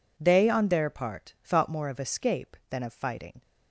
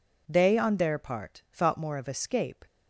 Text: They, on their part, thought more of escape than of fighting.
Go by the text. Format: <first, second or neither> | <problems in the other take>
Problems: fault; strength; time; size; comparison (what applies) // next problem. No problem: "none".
first | stops before "than of fighting"; at 2.6 s